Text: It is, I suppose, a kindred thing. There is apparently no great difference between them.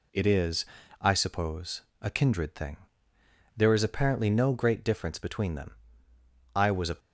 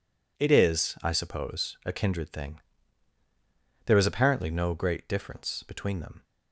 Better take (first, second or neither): second